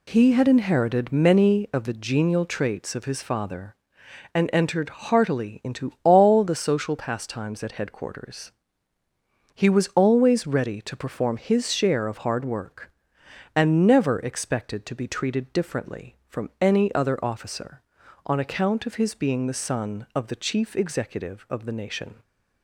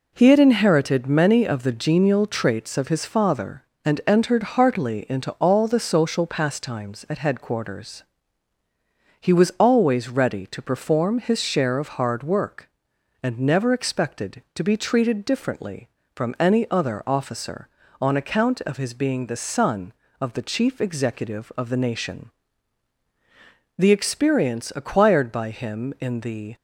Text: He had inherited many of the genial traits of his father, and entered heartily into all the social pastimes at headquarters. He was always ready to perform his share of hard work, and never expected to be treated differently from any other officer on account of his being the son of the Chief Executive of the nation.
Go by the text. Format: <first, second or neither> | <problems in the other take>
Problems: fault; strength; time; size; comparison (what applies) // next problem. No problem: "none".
first | goes on to say "The experience acquired by him in the"; strong; from 23.7 s on; 2.7 s long